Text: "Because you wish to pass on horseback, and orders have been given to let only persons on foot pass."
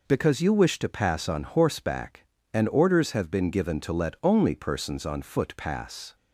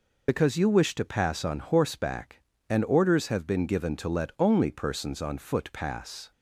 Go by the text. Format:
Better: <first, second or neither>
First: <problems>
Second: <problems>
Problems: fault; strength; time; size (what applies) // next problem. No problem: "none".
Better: first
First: none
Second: loses the start of "Because"; at 0.2 s; 55 ms